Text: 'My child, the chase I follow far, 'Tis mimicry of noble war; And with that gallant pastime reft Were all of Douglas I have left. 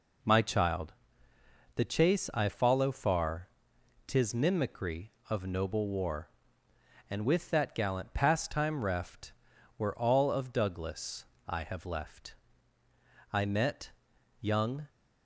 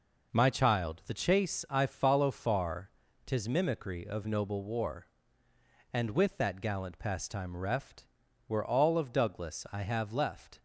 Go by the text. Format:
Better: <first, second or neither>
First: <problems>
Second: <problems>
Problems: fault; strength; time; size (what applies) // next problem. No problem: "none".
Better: second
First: pauses between "Douglas" and "I"; slight; at 11.2 s; 0.24 s long // goes on to say "I met young"; from 13.3 s on; 1.5 s long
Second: none